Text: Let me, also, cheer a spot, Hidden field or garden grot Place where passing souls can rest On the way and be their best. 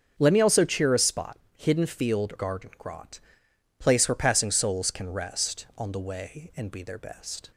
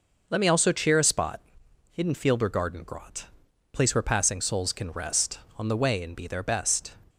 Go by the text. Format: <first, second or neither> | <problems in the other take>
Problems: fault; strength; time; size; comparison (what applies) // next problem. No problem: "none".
second | starts louder than the rest; strong; until 1.1 s; 7 dB // skips "or"; at 2.3 s // pauses between "grot" and "Place"; noticeable; at 3.2 s; 0.58 s long; noticeable in the second